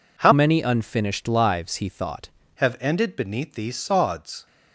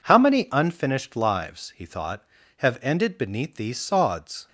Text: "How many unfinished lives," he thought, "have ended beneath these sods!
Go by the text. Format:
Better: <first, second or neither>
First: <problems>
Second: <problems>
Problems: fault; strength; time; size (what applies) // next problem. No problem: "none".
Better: second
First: changes voice from "many" to "thought"; from 0.3 to 2.2 s; 1.9 s long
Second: none